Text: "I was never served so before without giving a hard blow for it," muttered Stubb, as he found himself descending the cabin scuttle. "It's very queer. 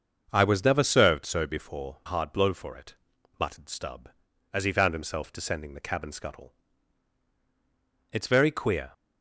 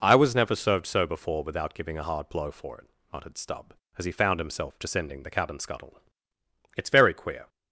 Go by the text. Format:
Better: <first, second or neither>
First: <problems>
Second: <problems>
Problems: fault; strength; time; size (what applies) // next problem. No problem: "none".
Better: second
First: starts louder than the rest; until 1.3 s; 6.5 dB // skips "without giving a"; at 2.0 s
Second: none